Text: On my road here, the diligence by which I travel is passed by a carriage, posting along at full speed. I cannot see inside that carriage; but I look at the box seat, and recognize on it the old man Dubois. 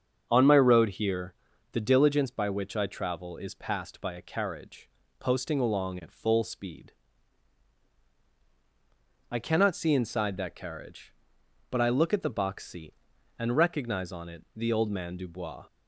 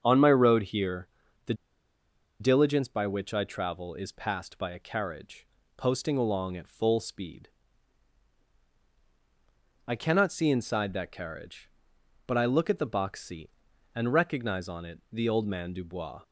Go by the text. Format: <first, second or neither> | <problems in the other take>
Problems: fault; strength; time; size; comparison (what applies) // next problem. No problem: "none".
first | starts louder than the rest; until 1.0 s; 7 dB; also in the first // pauses between "the" and "diligence"; noticeable; at 1.5 s; 0.86 s long